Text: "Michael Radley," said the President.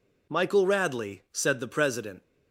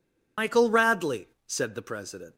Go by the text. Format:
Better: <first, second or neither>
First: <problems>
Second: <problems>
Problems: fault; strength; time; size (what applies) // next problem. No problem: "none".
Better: first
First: none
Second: loses the start of "Michael"; at 0.3 s; 115 ms